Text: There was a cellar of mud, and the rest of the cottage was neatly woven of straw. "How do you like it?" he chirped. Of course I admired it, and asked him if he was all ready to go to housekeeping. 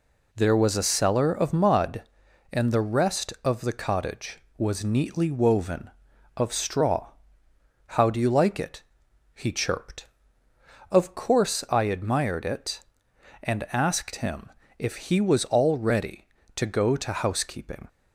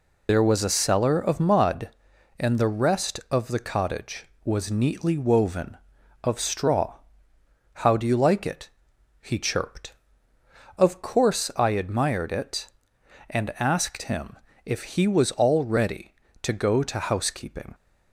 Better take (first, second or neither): first